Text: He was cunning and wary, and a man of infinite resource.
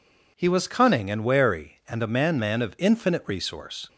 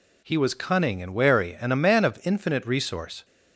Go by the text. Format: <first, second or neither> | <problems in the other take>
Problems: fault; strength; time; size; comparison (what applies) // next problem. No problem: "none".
second | says "man" twice; at 2.3 s